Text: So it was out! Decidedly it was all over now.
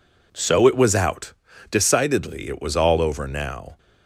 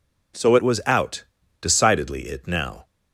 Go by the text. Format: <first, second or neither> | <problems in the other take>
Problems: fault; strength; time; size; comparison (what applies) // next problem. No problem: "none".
first | skips "was all over"; at 2.4 s